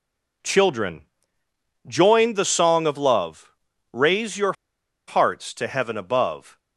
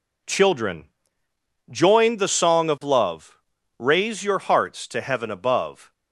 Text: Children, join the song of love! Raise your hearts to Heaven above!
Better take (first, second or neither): second